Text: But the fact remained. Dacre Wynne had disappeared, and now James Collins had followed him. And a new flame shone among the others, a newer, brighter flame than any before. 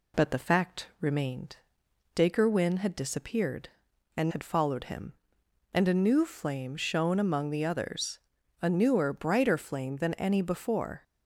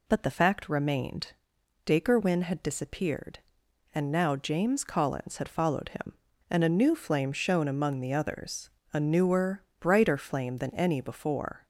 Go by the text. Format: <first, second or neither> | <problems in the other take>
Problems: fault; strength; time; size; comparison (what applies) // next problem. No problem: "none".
second | skips "now James Collins"; at 4.2 s